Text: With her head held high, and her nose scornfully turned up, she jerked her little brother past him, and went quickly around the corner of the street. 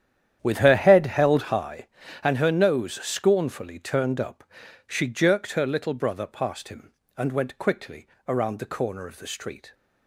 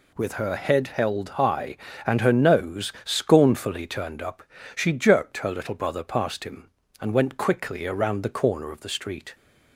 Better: second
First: starts louder than the rest; strong; until 1.7 s; 10 dB // pauses between "quickly" and "around"; slight; at 8.0 s; 0.18 s long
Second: none

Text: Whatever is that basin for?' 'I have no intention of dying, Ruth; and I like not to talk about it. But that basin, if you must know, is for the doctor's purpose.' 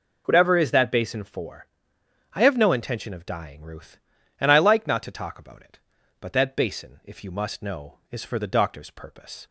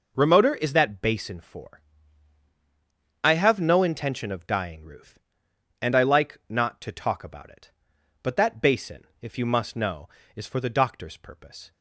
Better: first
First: none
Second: says "Remoter" for "Whatever"; at 0.1 s

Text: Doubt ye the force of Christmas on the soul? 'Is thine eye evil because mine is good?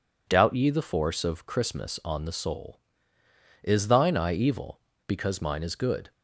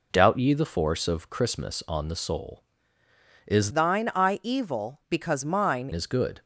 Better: first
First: none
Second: changes voice from "thine" to "mine"; from 3.7 to 5.8 s; 2.1 s long

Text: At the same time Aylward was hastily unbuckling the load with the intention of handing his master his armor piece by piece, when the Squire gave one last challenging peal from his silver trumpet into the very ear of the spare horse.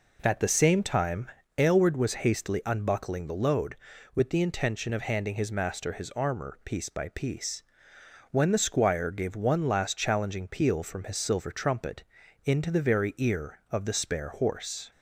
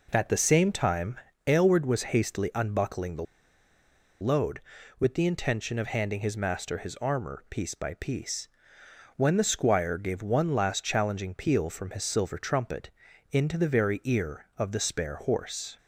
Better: first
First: pauses between "time" and "Aylward"; slight; at 1.3 s; 0.26 s long // pauses between "trumpet" and "into"; at 12.0 s; 0.42 s long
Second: pauses between "time" and "Aylward"; slight; at 1.1 s; 0.26 s long // pauses between "the" and "load"; noticeable; at 3.2 s; 0.97 s long // pauses between "trumpet" and "into"; at 12.8 s; 0.42 s long

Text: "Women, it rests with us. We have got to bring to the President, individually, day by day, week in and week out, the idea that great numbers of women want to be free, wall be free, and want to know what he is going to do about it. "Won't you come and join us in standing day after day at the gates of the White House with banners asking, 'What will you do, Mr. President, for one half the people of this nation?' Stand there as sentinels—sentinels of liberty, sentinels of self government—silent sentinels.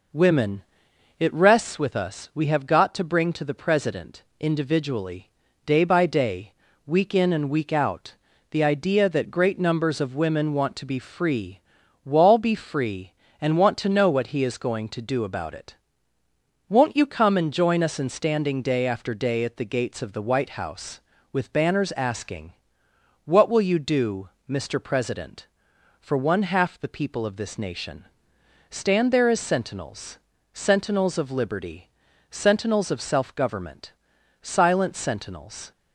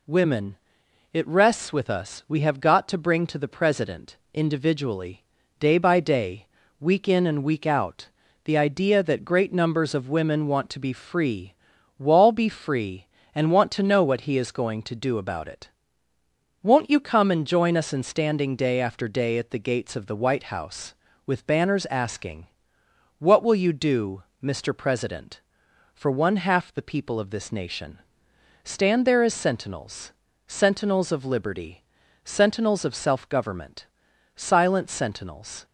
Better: second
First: starts louder than the rest; noticeable; until 1.6 s; 5 dB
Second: none

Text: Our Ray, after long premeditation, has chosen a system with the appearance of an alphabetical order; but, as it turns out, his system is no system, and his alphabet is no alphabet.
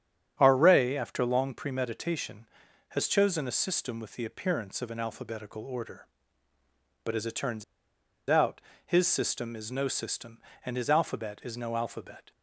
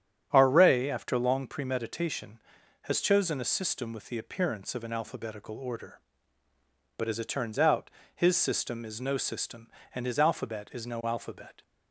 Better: second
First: starts louder than the rest; strong; until 1.3 s; 9 dB // pauses between "turns" and "out"; noticeable; at 7.6 s; 0.66 s long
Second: starts louder than the rest; strong; until 1.3 s; 9.5 dB

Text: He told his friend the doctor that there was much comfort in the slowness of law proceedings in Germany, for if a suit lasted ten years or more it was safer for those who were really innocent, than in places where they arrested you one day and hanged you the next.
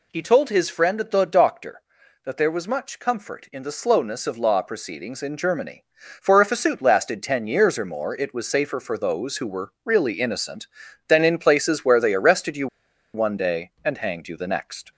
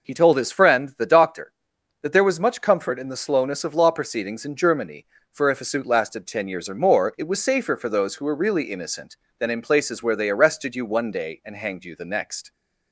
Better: second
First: pauses between "you" and "one"; noticeable; at 12.6 s; 0.48 s long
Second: none

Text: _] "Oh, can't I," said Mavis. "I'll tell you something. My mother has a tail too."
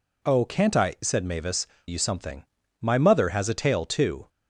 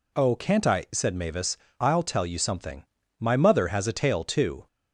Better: second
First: skips "I'll tell"; at 1.7 s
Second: none

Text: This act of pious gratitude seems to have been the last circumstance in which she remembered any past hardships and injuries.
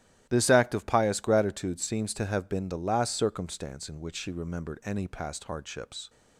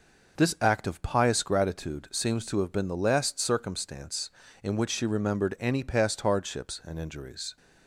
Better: second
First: starts louder than the rest; strong; until 1.3 s; 14 dB // stops before "and injuries"; at 6.0 s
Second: none

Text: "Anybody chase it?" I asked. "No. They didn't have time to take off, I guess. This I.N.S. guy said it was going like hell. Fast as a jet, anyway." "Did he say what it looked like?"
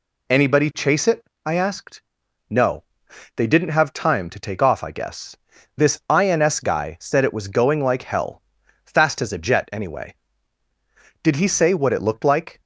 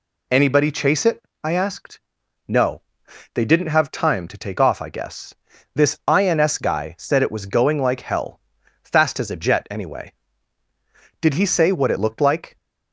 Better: neither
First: none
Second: none

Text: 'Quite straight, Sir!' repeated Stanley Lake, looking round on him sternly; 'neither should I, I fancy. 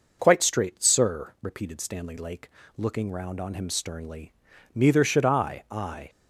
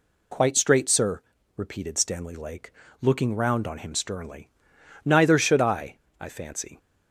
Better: second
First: stops before "fancy"; at 6.0 s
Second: none

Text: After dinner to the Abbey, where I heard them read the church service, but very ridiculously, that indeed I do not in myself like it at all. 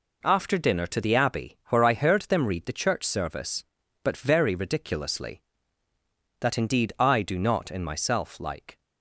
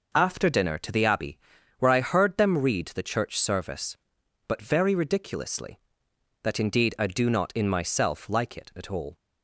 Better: second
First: stops before "it at all"; at 8.7 s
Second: none

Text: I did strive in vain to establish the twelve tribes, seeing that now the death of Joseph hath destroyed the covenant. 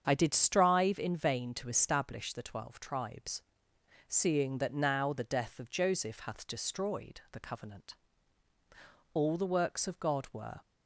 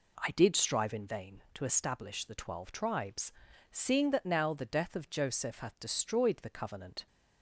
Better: second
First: starts louder than the rest; strong; until 1.0 s; 7.5 dB // goes on to say "All the works of God were"; from 9.1 s on; 1.4 s long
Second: none

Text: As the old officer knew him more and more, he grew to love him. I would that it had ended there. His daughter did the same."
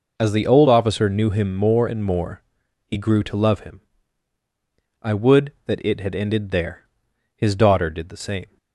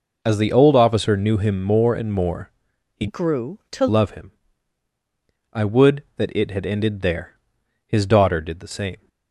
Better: first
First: none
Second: changes voice from "grew" to "to"; from 3.0 to 3.8 s; 0.8 s long

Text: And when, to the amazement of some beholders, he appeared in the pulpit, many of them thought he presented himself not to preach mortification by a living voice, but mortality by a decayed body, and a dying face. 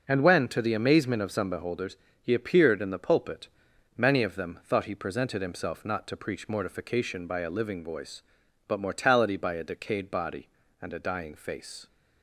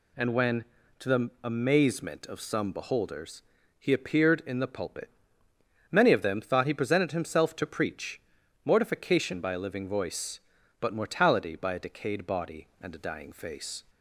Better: first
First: none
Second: skips "not"; at 7.5 s // pauses between "preach" and "mortification"; at 8.1 s; 0.44 s long

